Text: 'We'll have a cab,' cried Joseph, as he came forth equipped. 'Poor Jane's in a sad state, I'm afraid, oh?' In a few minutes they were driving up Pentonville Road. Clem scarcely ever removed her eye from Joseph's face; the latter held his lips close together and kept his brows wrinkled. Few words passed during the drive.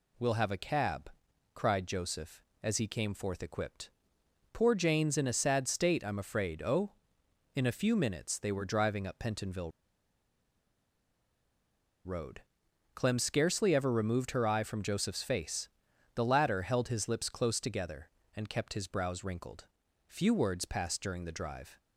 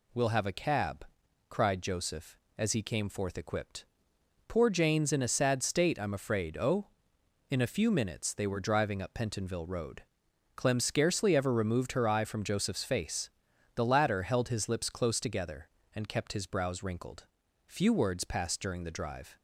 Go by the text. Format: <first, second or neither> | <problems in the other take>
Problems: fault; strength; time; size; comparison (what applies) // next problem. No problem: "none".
second | pauses between "Pentonville" and "Road"; strong; at 9.7 s; 2.3 s long